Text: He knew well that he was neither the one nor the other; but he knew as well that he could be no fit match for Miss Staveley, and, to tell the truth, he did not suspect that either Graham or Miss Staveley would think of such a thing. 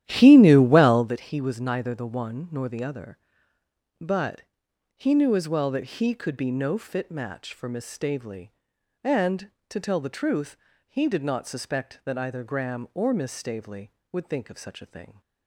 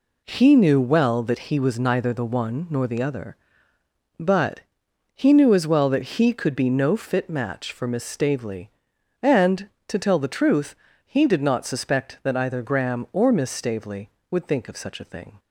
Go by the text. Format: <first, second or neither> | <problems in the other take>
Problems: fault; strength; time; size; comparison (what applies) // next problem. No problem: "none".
second | starts louder than the rest; strong; until 1.1 s; 12 dB // pauses between "but" and "he"; noticeable; at 4.4 s; 0.54 s long; noticeable in the second